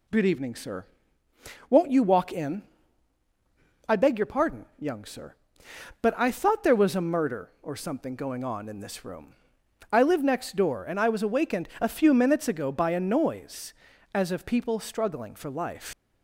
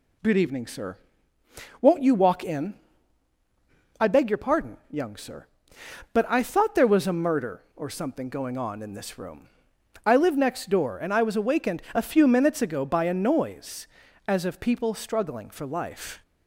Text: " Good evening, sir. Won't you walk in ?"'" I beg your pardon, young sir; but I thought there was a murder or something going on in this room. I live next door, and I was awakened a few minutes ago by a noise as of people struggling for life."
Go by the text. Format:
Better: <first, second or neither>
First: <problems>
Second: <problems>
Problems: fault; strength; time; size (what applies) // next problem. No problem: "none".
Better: second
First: leaves "life" unfinished; at 15.9 s; 125 ms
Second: none